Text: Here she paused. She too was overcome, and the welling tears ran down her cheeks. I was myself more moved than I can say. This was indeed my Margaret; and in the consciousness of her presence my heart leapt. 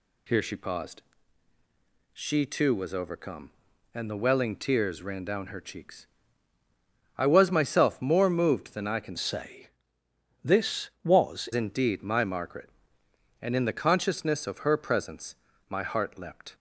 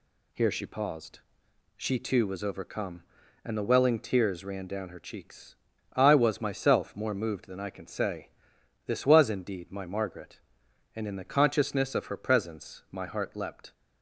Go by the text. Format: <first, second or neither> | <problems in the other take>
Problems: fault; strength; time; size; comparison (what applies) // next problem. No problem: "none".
second | changes voice from "say" to "was"; from 9.1 to 11.4 s; 2.3 s long // pauses between "presence" and "my"; slight; at 15.3 s; 0.34 s long